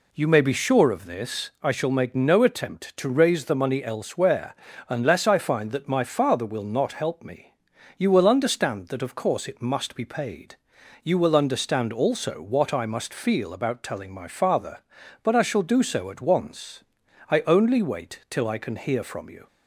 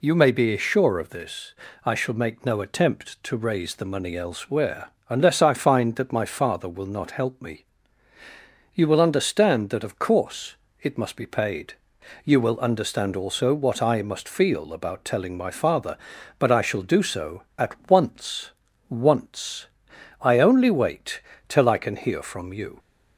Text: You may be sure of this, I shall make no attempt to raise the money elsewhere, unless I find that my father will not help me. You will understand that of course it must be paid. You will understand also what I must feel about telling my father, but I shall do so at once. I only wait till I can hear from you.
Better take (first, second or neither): first